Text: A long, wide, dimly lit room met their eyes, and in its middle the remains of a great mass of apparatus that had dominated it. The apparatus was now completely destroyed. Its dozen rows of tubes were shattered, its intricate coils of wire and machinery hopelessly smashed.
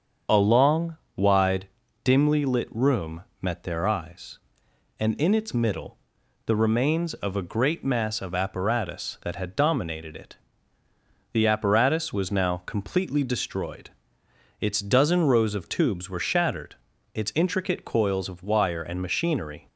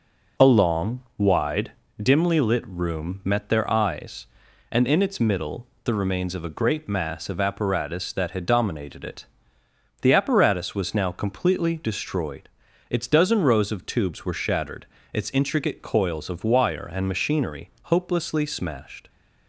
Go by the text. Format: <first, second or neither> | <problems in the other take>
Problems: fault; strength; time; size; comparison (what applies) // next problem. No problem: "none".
second | starts louder than the rest; strong; until 1.5 s; 7 dB // pauses between "room" and "met"; slight; at 3.2 s; 0.18 s long // pauses between "middle" and "the"; noticeable; at 5.9 s; 0.48 s long; slight in the second // stops before "hopelessly smashed"; at 19.6 s